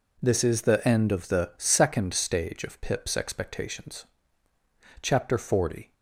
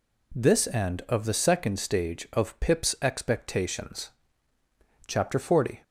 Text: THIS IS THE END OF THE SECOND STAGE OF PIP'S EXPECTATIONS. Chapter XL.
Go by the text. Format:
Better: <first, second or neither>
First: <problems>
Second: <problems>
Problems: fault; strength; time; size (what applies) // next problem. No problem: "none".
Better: first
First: none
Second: skips "IS THE"; at 0.6 s